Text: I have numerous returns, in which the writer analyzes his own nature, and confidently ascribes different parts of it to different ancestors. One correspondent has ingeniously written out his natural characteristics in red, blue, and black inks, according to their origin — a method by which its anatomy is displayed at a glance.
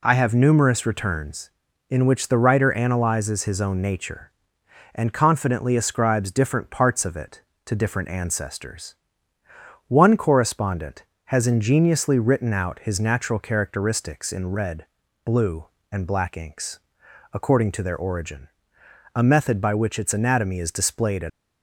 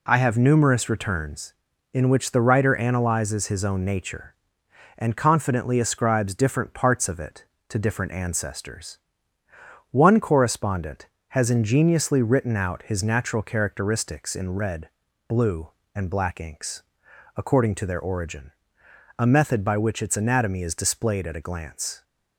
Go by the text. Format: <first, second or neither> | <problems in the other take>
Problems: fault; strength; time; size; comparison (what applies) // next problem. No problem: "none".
second | stops before "a glance"; at 21.2 s